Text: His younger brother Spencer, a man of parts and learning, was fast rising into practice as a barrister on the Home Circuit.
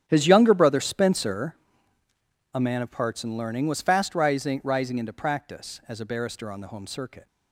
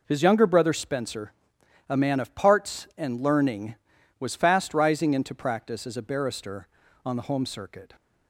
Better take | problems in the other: second | starts louder than the rest; strong; until 1.0 s; 10 dB // says "rising" twice; at 4.6 s

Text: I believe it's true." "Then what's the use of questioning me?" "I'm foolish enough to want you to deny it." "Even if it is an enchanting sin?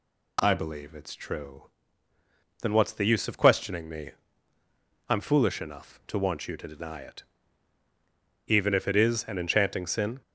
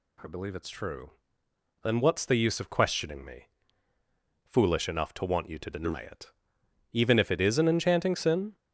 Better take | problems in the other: first | skips "I'm"; at 3.9 s

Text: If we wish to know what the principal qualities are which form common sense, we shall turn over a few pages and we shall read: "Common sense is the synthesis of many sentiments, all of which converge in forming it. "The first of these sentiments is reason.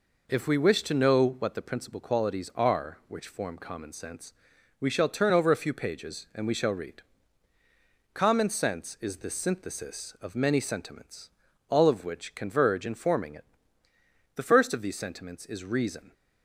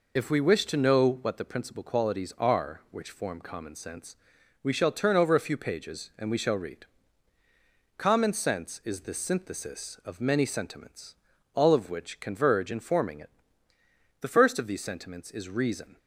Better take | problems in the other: first | loses the start of "If"; at 0.1 s; 50 ms

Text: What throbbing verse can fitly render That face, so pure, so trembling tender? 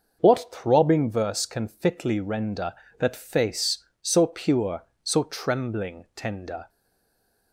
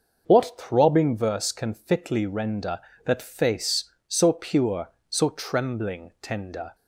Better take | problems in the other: second | starts louder than the rest; noticeable; until 1.2 s; 6 dB; noticeable in the second // stays silent after the last word; slight; from 6.6 s on; 0.9 s long

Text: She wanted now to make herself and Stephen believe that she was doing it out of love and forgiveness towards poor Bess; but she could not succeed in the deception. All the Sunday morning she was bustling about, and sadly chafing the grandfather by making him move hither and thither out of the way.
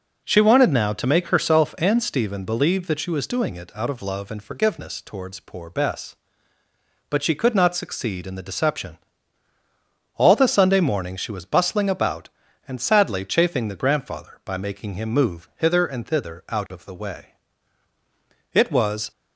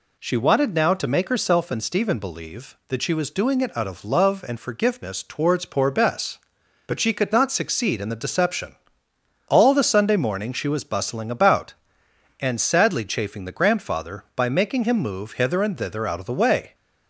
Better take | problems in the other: second | goes on to say "It was"; from 18.5 s on; 0.58 s long

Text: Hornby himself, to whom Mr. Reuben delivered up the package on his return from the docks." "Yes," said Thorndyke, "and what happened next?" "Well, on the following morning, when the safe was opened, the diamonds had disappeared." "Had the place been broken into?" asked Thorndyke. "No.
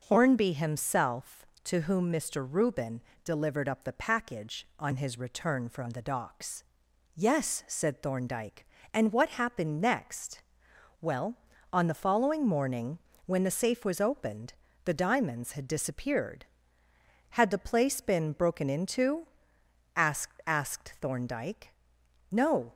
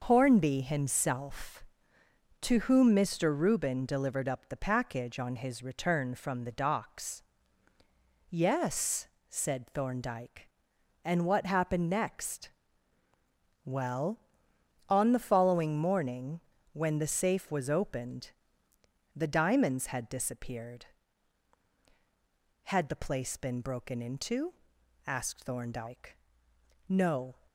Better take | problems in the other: second | pauses between "Reuben" and "delivered"; slight; at 3.0 s; 0.22 s long // says "asked" twice; at 20.4 s

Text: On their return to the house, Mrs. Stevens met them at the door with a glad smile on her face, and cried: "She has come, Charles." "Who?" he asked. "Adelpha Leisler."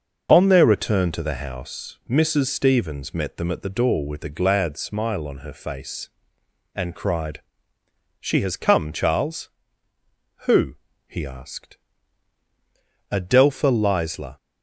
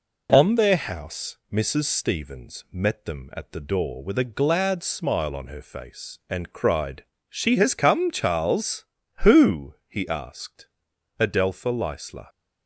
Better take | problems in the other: first | skips "return to the"; at 0.7 s

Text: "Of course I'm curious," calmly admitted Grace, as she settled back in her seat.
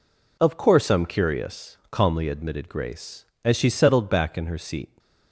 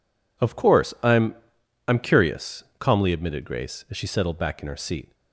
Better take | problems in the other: first | says "I'm" twice; at 1.8 s

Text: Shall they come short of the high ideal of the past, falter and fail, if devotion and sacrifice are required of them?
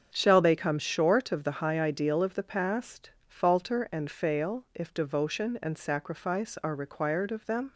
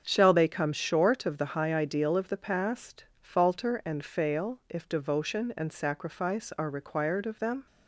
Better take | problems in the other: neither | starts louder than the rest; strong; the same in both

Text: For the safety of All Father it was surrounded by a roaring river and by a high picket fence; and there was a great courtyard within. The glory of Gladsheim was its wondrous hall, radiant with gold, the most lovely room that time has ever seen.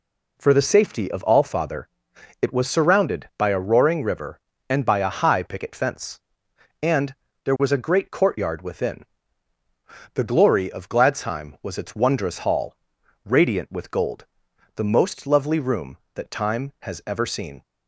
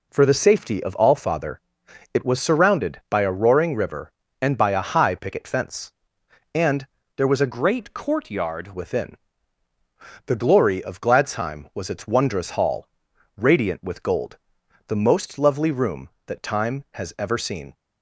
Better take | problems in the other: first | pauses between "Father" and "it"; noticeable; at 1.6 s; 0.54 s long; noticeable in the first // pauses between "and" and "there"; slight; at 6.8 s; 0.30 s long; slight in the first // changes voice from "great" to "courtyard"; from 7.5 to 8.7 s; 1.2 s long

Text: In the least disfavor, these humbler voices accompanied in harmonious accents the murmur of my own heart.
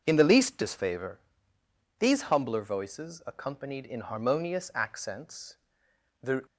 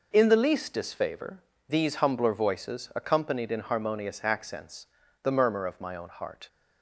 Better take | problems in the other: second | pauses between "accents" and "the"; noticeable; at 5.5 s; 0.66 s long; also in the second // stops before "murmur of my own heart"; at 6.4 s

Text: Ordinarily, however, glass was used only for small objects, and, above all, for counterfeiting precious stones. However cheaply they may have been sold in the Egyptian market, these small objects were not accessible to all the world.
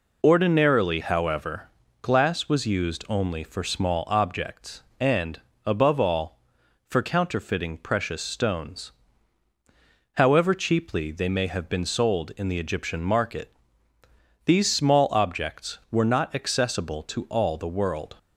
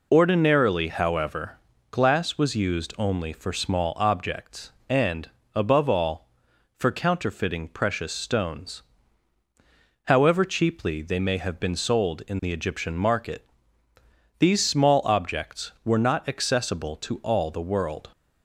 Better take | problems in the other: neither | none

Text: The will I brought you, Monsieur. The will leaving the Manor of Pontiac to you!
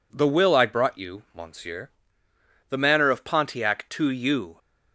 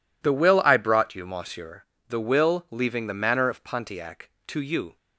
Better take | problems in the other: second | skips "will leaving the"; at 2.7 s

